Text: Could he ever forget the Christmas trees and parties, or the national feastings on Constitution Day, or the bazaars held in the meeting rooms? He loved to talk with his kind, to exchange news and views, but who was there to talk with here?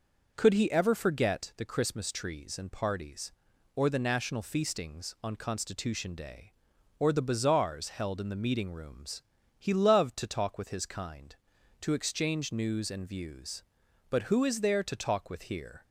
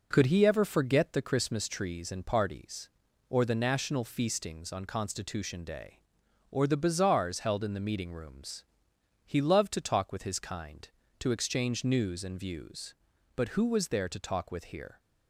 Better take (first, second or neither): second